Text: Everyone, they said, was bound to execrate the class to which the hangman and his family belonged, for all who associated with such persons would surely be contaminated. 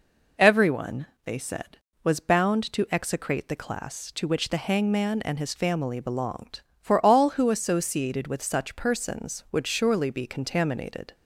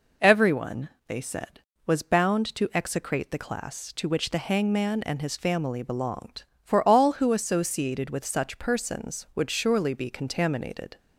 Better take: neither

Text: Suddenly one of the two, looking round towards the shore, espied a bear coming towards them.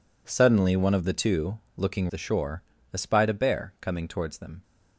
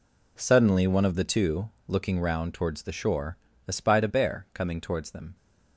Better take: second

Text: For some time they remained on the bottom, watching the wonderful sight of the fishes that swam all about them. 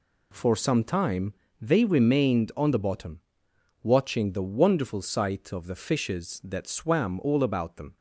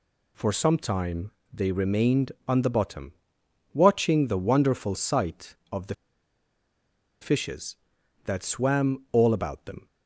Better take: first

